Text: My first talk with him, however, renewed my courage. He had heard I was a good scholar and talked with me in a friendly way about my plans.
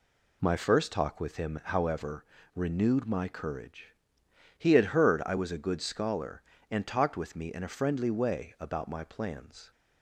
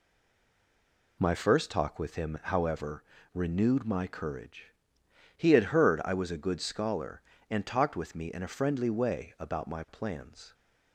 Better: first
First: none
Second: stays silent before the first word; noticeable; until 1.1 s; 1.1 s long

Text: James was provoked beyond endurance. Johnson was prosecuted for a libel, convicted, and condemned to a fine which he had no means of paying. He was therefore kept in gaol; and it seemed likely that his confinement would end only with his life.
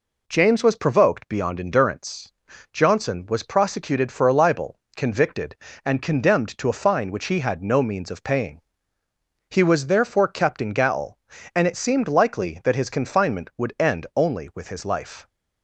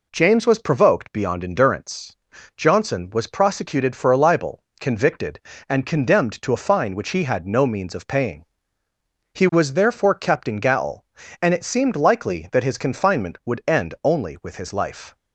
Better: neither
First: none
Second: none

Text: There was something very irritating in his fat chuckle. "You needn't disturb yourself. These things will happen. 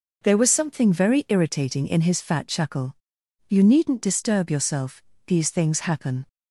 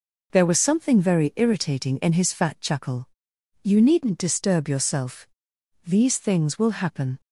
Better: second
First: skips "will"; at 5.7 s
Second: none

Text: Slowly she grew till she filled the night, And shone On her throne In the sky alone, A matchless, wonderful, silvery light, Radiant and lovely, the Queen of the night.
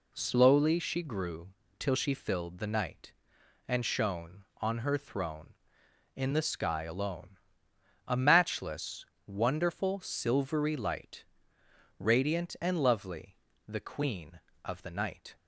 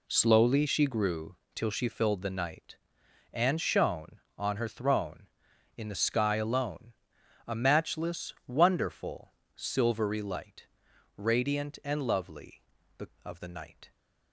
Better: first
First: pauses between "grew" and "till"; slight; at 1.5 s; 0.26 s long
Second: pauses between "grew" and "till"; slight; at 1.3 s; 0.18 s long // skips "Queen"; at 13.1 s

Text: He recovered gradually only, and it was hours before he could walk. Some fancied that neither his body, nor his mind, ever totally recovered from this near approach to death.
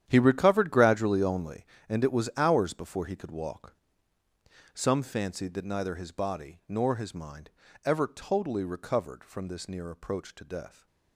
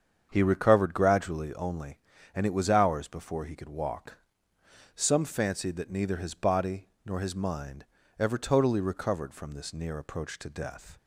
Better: second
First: gets quieter; strong; throughout; 13.5 dB // starts louder than the rest; strong; until 1.1 s; 10 dB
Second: starts louder than the rest; strong; until 1.3 s; 7.5 dB

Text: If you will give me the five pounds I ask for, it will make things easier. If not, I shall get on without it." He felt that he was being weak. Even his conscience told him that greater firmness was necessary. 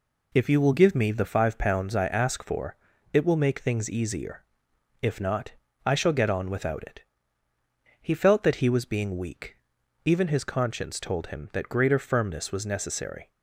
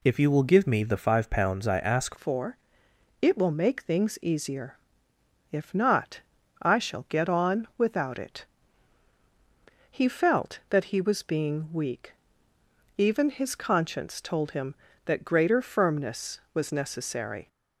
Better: first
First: none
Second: changes voice at "for"; from 2.1 s on; 15.3 s long

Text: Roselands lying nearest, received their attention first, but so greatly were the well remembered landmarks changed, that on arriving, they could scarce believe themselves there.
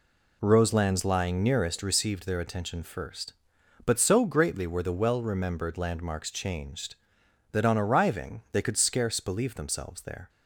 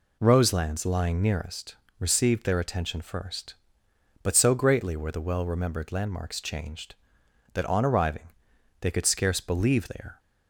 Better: first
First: none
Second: skips "themselves"; at 9.8 s

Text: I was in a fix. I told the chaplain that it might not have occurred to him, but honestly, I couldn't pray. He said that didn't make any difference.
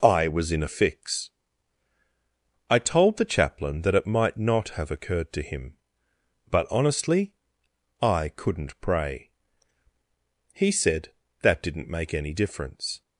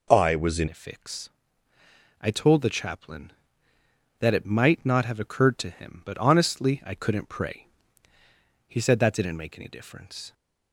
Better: first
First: none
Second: changes voice at "a"; from 0.6 s on; 9.7 s long

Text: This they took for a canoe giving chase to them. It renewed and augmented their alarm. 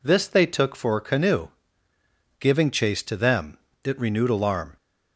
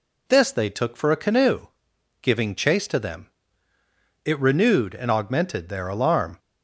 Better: second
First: pauses between "canoe" and "giving"; noticeable; at 1.4 s; 0.92 s long // skips "and augmented their"; at 4.3 s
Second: pauses between "canoe" and "giving"; noticeable; at 1.6 s; 0.52 s long

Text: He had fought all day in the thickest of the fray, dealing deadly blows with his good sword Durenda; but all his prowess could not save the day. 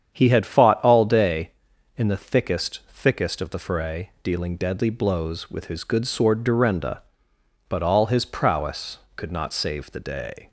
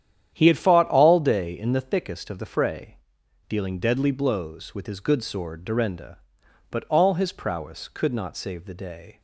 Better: second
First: starts louder than the rest; strong; until 1.1 s; 8.5 dB // says "thickest" twice; at 2.9 s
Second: starts louder than the rest; strong; until 1.3 s; 10 dB

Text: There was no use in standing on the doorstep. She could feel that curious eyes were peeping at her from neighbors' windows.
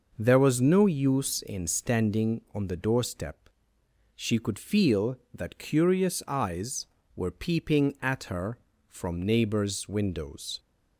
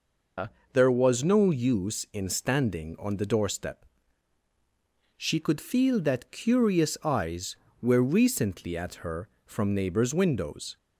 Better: first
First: none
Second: says "recently" for "peeping"; at 8.1 s

